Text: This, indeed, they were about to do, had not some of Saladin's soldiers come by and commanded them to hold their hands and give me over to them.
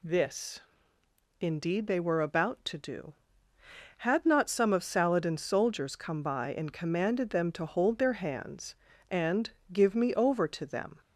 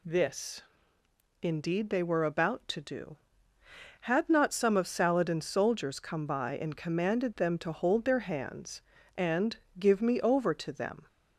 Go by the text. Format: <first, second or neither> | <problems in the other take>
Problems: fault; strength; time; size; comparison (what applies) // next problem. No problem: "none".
neither | pauses between "and" and "give"; slight; the same in both